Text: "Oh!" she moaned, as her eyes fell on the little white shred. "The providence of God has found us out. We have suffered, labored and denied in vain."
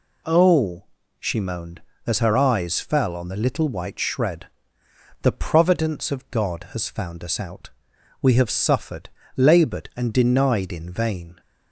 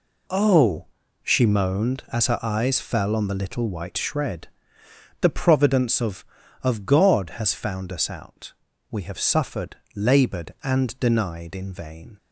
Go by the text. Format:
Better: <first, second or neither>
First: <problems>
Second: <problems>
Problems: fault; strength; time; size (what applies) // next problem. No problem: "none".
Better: first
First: none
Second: says "of" twice; at 6.6 s